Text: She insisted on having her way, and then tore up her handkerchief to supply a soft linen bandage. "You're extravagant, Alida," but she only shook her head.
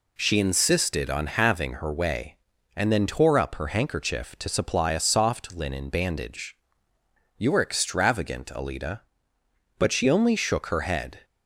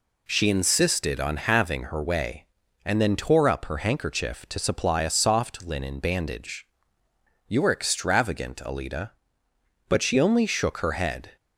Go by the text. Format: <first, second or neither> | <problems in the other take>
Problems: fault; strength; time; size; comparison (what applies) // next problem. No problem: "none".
neither | none